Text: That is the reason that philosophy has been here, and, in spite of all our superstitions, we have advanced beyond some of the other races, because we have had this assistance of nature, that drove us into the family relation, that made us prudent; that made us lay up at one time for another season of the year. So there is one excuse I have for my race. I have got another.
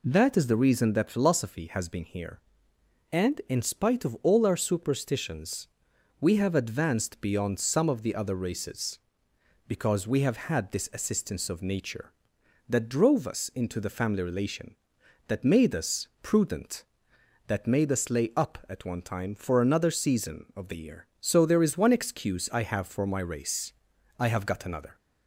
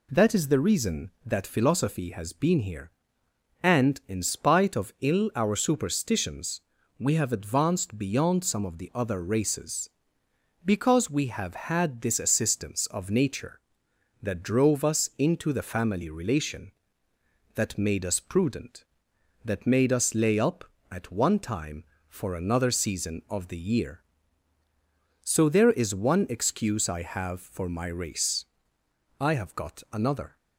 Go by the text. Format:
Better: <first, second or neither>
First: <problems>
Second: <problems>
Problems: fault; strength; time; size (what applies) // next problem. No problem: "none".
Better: first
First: none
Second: says "ill" for "all"; at 5.0 s